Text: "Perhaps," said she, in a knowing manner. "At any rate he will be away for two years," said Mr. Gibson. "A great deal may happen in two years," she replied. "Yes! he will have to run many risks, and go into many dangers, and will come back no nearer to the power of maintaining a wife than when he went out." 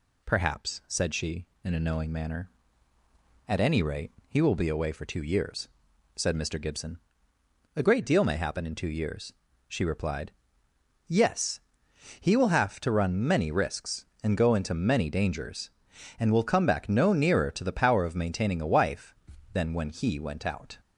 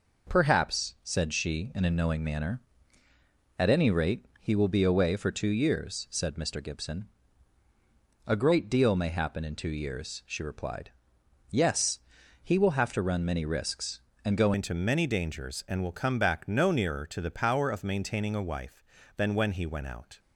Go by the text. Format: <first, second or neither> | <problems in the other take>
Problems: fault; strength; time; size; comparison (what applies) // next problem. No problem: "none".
first | pauses between "rate" and "he"; slight; at 4.2 s; 0.16 s long; slight in the first // changes voice at "into"; from 14.5 s on; 5.6 s long